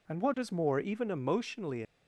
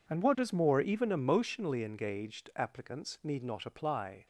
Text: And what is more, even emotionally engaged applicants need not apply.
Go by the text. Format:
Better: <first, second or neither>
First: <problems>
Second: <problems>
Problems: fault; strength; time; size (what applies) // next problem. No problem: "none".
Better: second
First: stops before "engaged applicants need not apply"; at 1.8 s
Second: none